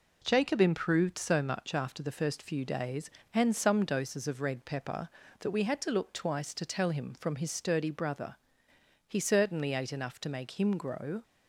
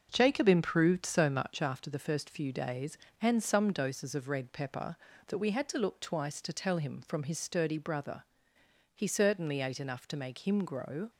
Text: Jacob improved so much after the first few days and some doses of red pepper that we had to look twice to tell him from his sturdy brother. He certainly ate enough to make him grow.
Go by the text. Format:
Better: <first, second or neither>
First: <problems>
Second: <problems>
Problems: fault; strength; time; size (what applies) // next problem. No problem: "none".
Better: first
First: none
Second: starts louder than the rest; until 1.8 s; 6 dB